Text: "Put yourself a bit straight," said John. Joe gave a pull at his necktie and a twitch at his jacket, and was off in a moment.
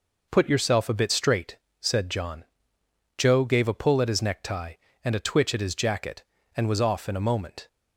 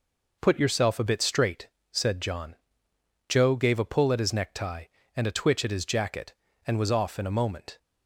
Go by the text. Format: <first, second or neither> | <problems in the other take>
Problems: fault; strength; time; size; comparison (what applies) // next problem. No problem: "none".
neither | none